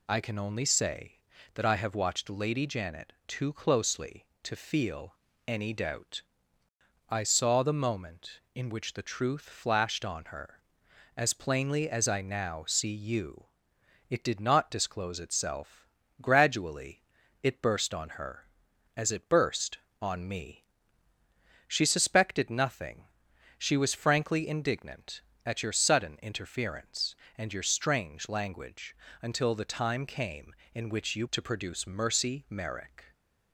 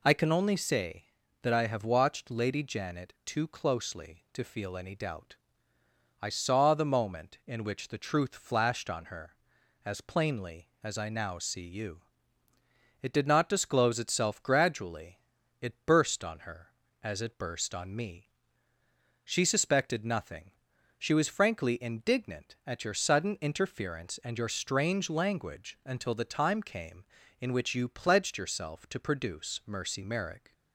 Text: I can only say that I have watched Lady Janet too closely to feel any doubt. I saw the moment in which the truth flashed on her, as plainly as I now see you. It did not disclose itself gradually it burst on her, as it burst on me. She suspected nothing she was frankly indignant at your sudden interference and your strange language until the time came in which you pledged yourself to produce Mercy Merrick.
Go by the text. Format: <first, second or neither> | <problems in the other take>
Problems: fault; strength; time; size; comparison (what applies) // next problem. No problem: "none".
second | pauses between "feel" and "any"; slight; at 5.1 s; 0.32 s long // pauses between "itself" and "gradually"; slight; at 15.8 s; 0.34 s long // pauses between "gradually" and "it"; at 17.0 s; 0.40 s long; also in the second // pauses between "nothing" and "she"; noticeable; at 23.0 s; 0.54 s long; noticeable in the second // pauses between "language" and "until"; slight; at 28.9 s; 0.26 s long // skips "pledged yourself"; at 31.2 s